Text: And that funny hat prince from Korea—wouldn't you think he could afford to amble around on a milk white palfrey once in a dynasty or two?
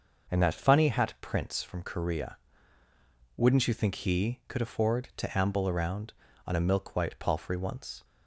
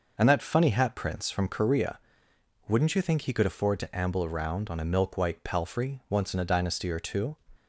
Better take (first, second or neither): second